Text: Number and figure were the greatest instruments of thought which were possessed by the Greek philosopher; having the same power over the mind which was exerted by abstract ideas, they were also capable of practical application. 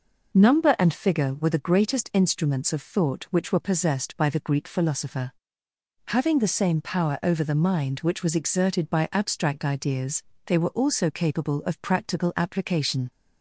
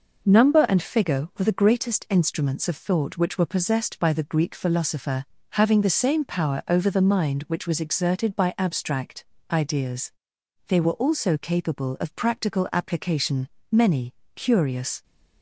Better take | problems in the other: first | pauses between "abstract" and "ideas"; slight; at 9.2 s; 0.26 s long // goes on to say "Many curious"; from 13.7 s on; 1.3 s long

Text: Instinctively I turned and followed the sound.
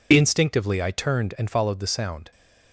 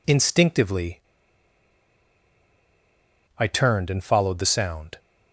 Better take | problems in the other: first | pauses between "Instinctively" and "I"; strong; at 1.0 s; 2.3 s long

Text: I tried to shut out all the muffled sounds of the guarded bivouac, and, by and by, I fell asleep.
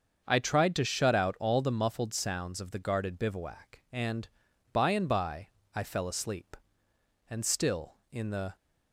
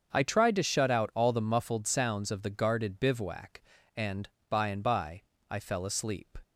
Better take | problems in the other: second | starts louder than the rest; until 1.2 s; 7 dB; also in the second // goes on to say "And still in the"; noticeable; from 7.2 s on; 1.2 s long

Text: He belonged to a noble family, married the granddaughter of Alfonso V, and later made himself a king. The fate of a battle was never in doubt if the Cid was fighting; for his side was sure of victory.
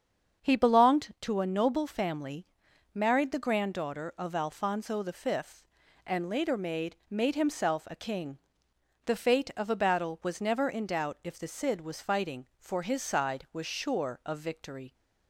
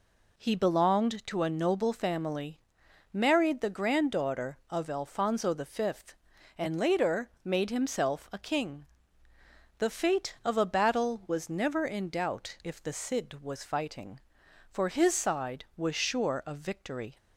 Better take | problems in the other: second | starts louder than the rest; strong; until 1.4 s; 7.5 dB // says "made" twice; at 7.0 s

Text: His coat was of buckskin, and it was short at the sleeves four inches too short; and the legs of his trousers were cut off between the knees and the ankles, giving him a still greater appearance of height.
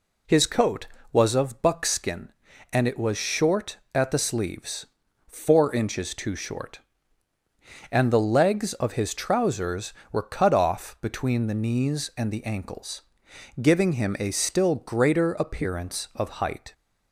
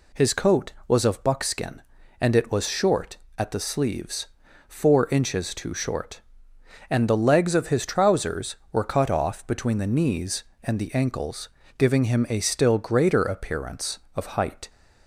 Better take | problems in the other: neither | pauses between "sleeves" and "four"; the same in both

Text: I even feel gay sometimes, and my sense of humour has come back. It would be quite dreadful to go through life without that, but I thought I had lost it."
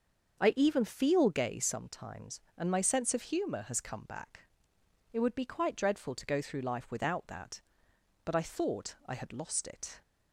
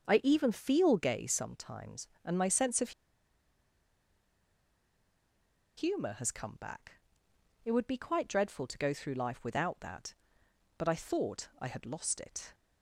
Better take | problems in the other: first | starts louder than the rest; until 1.0 s; 6.5 dB; also in the first // pauses between "of" and "humour"; strong; at 2.9 s; 2.8 s long

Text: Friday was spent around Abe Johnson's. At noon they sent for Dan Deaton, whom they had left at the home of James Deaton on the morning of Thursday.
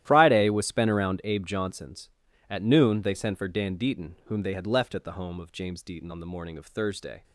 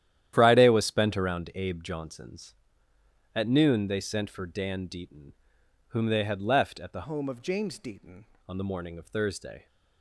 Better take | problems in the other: first | starts louder than the rest; strong; until 1.3 s; 11.5 dB; strong in the first // changes voice from "home" to "Deaton"; from 7.0 to 8.2 s; 1.2 s long

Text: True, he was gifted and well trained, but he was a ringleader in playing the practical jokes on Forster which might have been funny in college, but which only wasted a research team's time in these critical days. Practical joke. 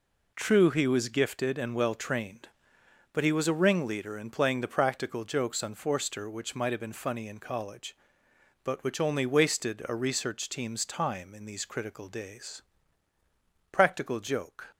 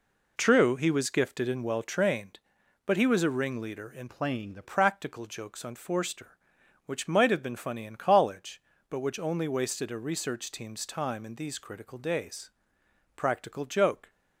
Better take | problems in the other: first | changes voice from "playing" to "the"; from 4.0 to 4.6 s; 0.6 s long

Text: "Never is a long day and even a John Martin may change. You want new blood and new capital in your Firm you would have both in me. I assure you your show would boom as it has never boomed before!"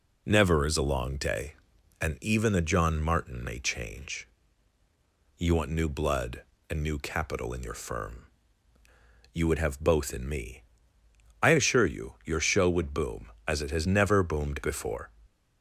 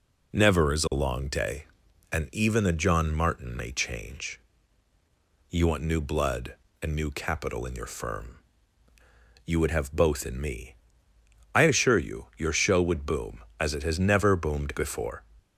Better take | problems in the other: neither | pauses between "Firm" and "you"; the same in both

